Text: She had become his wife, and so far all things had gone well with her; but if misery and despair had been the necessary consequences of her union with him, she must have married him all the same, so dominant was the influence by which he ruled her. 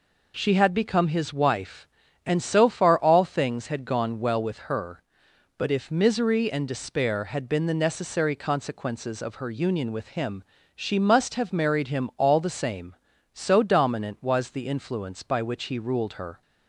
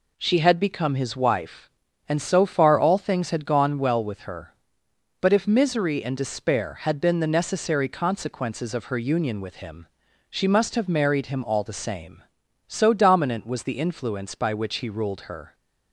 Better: neither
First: none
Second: none

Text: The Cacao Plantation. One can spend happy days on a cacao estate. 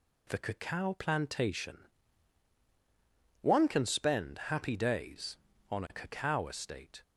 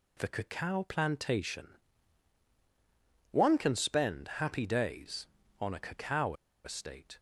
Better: first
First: none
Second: pauses between "cacao" and "estate"; slight; at 6.3 s; 0.30 s long

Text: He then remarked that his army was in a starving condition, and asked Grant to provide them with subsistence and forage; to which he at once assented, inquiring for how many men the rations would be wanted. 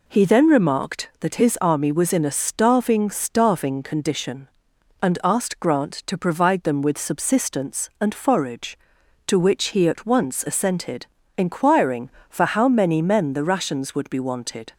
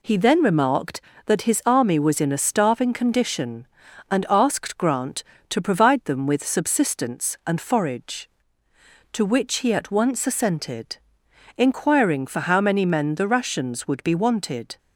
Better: second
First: says "starving" twice; at 3.0 s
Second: none

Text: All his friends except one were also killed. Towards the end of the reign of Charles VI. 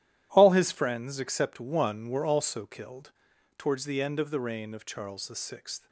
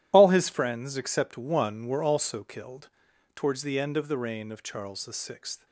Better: first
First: starts louder than the rest; strong; until 1.3 s; 12.5 dB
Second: loses the start of "All"; at 0.1 s; 45 ms // starts louder than the rest; strong; until 1.1 s; 12.5 dB

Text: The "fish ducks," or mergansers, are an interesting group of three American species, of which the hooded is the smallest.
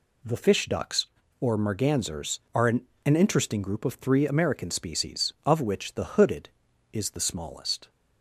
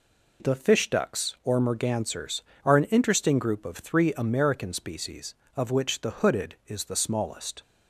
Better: second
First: says "an" twice; at 3.0 s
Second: none

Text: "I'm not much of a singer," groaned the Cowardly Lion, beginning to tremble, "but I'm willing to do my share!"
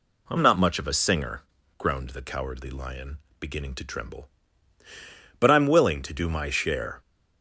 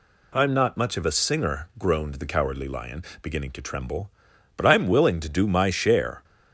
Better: neither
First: none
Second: none

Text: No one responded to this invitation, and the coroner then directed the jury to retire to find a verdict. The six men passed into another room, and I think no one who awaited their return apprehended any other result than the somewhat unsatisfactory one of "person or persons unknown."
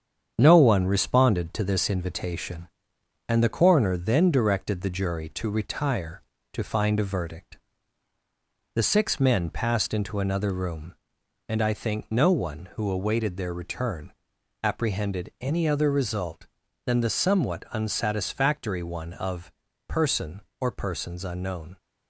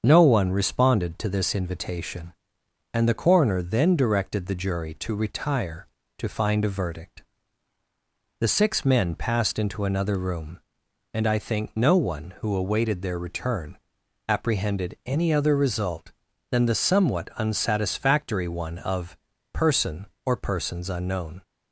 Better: second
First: gets quieter; noticeable; throughout; 4.5 dB // starts louder than the rest; strong; until 1.3 s; 8 dB // pauses between "return" and "apprehended"; noticeable; at 14.1 s; 0.50 s long // pauses between "of" and "person"; slight; at 19.5 s; 0.34 s long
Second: starts louder than the rest; until 1.0 s; 7 dB // pauses between "return" and "apprehended"; noticeable; at 13.7 s; 0.50 s long // pauses between "of" and "person"; slight; at 19.1 s; 0.34 s long

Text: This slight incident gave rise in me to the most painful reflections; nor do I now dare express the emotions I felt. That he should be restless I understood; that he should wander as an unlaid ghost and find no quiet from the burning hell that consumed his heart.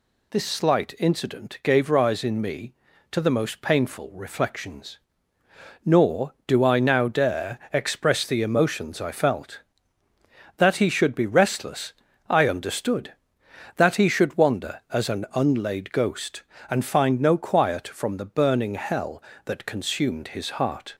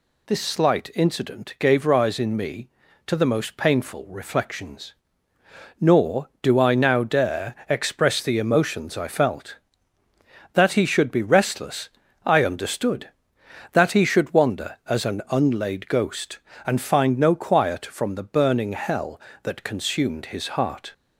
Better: neither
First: pauses between "dare" and "express"; slight; at 7.5 s; 0.16 s long // pauses between "restless" and "I"; slight; at 11.9 s; 0.34 s long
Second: pauses between "dare" and "express"; slight; at 7.5 s; 0.16 s long // pauses between "restless" and "I"; slight; at 11.8 s; 0.34 s long

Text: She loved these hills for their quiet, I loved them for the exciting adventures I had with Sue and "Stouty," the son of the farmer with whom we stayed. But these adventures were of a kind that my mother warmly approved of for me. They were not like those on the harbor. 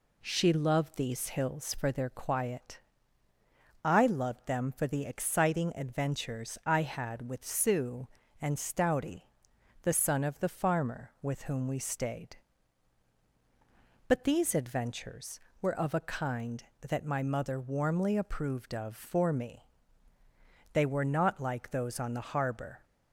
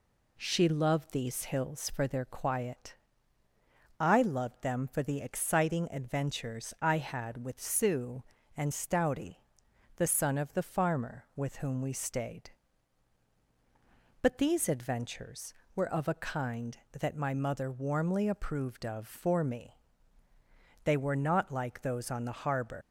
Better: first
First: none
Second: leaves "harbor" unfinished; at 22.8 s; 135 ms

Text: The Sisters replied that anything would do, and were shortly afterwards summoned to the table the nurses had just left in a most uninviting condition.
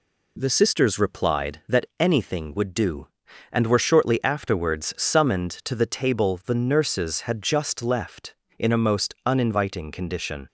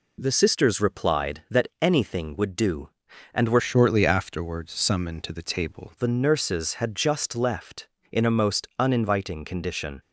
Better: first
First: none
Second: changes voice from "shortly" to "table"; from 3.5 to 5.9 s; 2.4 s long

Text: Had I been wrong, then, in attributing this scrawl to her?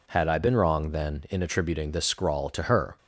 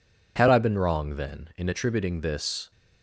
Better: first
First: none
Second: stops before "scrawl to her"; at 2.7 s

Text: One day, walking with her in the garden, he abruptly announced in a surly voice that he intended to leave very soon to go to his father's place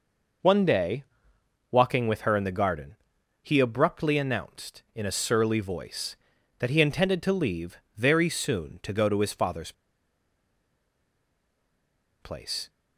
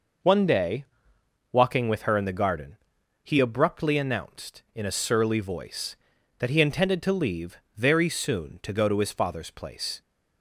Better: second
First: pauses between "leave" and "very"; slight; at 7.7 s; 0.18 s long // pauses between "father's" and "place"; strong; at 9.7 s; 2.4 s long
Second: pauses between "leave" and "very"; slight; at 7.5 s; 0.18 s long

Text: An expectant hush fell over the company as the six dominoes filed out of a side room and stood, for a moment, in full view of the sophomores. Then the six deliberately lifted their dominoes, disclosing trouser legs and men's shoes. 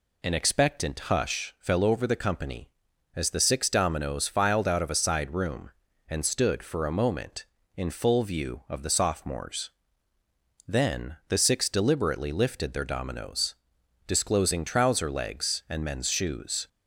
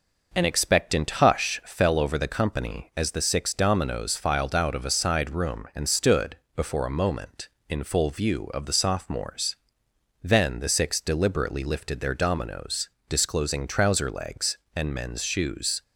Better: first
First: none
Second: says "before" for "for"; at 6.5 s

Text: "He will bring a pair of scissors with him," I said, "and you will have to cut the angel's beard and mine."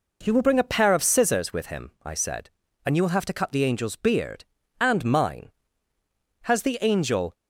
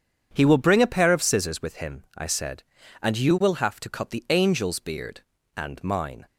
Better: second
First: goes on to say "Has the angel"; noticeable; from 6.4 s on; 0.92 s long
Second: none

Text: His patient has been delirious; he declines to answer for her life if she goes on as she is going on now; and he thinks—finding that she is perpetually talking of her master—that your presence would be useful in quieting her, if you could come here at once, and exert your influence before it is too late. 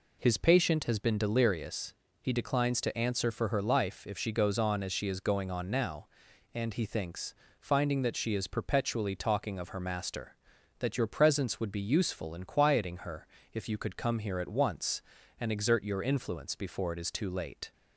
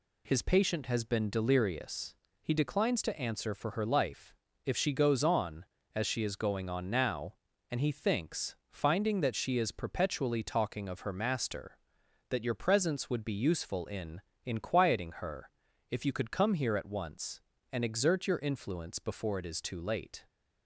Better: first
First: none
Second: pauses between "life" and "if"; slight; at 4.3 s; 0.30 s long // says "in" twice; at 14.4 s

